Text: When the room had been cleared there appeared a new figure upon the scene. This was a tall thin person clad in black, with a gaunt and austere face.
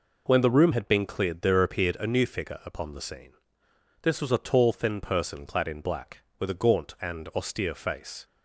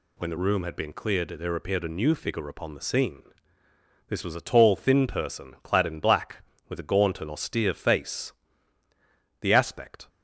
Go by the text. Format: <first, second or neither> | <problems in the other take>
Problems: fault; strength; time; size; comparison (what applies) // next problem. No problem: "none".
first | goes on to say "The aspect"; noticeable; from 9.4 s on; 0.66 s long